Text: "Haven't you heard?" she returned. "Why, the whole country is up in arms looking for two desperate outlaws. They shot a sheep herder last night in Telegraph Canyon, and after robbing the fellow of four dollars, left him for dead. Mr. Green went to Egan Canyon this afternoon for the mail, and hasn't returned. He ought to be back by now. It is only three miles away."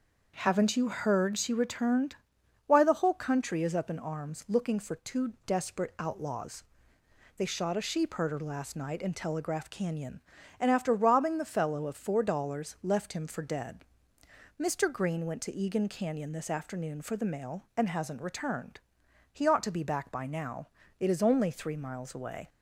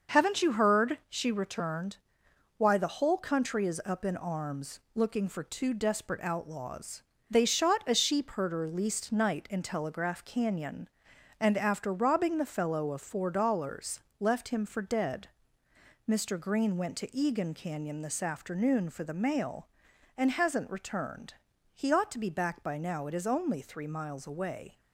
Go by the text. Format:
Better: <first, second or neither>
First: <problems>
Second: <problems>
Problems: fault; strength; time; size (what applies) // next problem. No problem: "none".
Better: first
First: starts louder than the rest; noticeable; until 1.3 s; 6 dB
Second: starts louder than the rest; noticeable; until 1.2 s; 6 dB // pauses between "arms" and "looking"; slight; at 4.7 s; 0.16 s long // says "least" for "last"; at 8.6 s